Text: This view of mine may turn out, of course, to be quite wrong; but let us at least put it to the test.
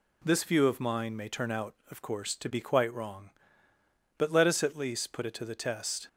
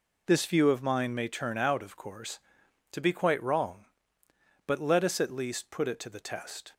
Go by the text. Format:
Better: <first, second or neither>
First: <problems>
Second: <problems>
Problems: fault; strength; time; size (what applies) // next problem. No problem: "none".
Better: neither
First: none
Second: none